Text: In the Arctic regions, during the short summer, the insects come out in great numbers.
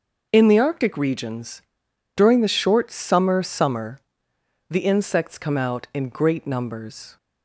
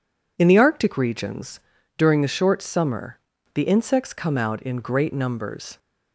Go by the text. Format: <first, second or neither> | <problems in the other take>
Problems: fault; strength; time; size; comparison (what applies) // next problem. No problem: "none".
second | says "summer" twice; at 3.4 s